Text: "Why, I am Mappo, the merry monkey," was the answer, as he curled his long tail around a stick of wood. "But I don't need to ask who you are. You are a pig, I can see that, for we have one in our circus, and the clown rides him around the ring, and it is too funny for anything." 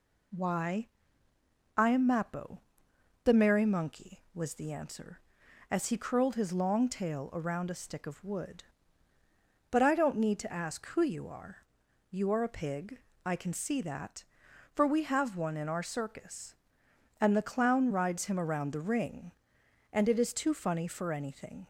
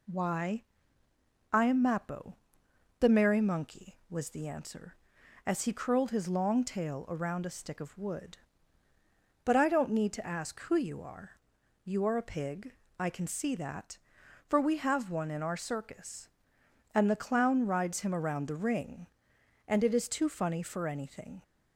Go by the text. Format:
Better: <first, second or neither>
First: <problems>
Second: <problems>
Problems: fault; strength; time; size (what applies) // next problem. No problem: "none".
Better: neither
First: none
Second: none